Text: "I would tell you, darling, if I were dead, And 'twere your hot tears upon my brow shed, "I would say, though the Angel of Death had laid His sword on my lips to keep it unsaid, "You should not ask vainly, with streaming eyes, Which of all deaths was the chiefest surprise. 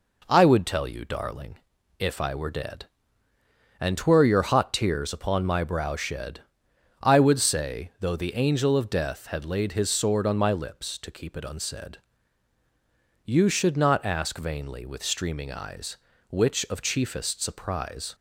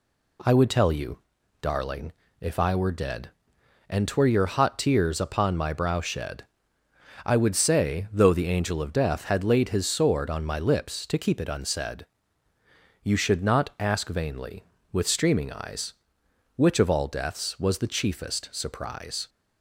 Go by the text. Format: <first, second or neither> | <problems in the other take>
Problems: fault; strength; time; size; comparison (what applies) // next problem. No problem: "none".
second | skips "all deaths was the"; at 16.8 s